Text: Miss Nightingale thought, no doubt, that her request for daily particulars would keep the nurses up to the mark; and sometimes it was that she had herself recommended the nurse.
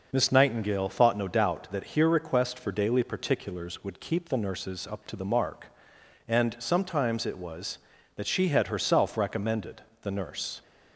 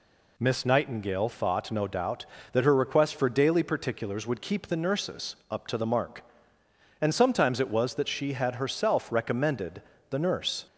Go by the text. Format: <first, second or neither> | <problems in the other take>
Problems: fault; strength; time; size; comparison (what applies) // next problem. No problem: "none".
second | says "here" for "her"; at 1.8 s // pauses between "recommended" and "the"; slight; at 9.8 s; 0.20 s long; slight in the second